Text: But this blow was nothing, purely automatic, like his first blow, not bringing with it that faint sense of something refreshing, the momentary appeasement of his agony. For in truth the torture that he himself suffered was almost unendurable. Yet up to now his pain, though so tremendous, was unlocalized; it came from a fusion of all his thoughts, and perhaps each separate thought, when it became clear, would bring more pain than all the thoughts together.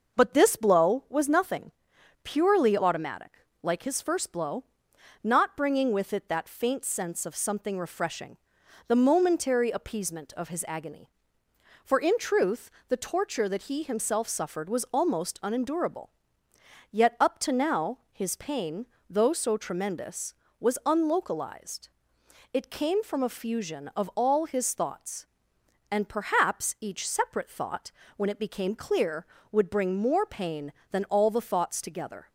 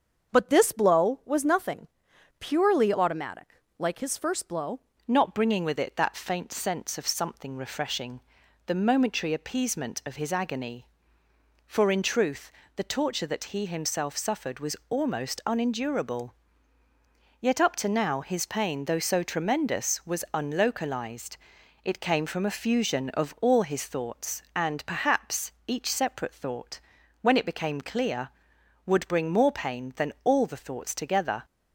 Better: first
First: pauses between "truth" and "the"; slight; at 12.6 s; 0.20 s long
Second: starts louder than the rest; until 1.3 s; 6.5 dB // changes voice at "not"; from 5.0 s on; 26.4 s long // pauses between "truth" and "the"; slight; at 12.5 s; 0.24 s long // pauses between "perhaps" and "each"; slight; at 25.5 s; 0.16 s long

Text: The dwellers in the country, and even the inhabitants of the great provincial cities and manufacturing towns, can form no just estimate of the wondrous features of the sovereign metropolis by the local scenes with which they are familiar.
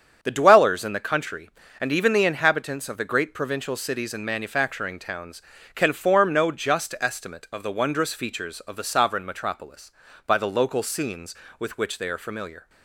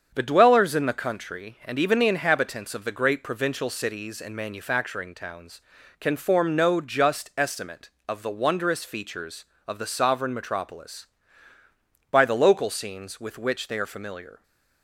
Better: neither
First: starts louder than the rest; strong; until 1.2 s; 7.5 dB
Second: starts louder than the rest; strong; until 1.1 s; 7 dB

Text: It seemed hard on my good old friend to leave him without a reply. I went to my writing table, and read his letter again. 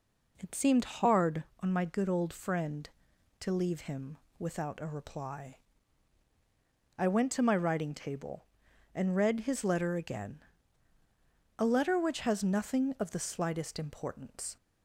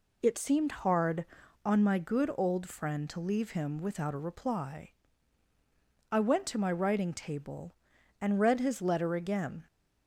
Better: second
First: pauses between "him" and "without"; slight; at 4.1 s; 0.20 s long // goes on to say "A letter which has nothing of the slightest importance"; strong; from 11.5 s on; 2.9 s long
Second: none

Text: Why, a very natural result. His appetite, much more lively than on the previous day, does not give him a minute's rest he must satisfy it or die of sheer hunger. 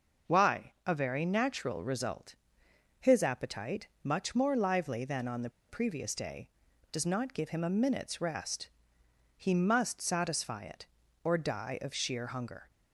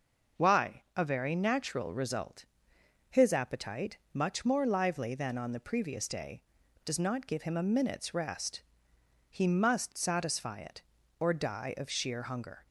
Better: second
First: pauses between "the" and "previous"; slight; at 5.4 s; 0.19 s long // pauses between "rest" and "he"; noticeable; at 8.6 s; 0.68 s long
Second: pauses between "rest" and "he"; noticeable; at 8.6 s; 0.68 s long

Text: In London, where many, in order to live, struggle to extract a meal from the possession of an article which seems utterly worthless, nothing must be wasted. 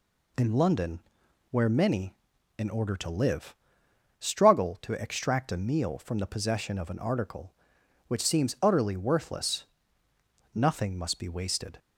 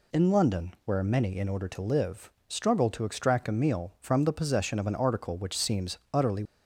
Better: first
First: none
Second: stops before "worthless nothing must be wasted"; at 6.4 s

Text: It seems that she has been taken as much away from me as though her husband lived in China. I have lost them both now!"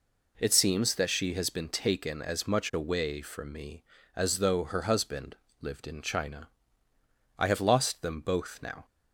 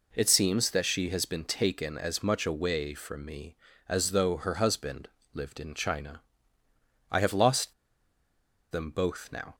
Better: first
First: pauses between "husband" and "lived"; slight; at 5.3 s; 0.26 s long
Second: pauses between "husband" and "lived"; slight; at 5.0 s; 0.26 s long // pauses between "lost" and "them"; noticeable; at 7.7 s; 0.97 s long

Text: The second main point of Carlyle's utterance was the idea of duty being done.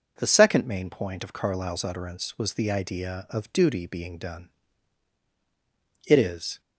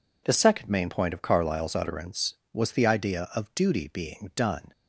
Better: second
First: goes on to say "It is"; from 6.0 s on; 0.53 s long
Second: none

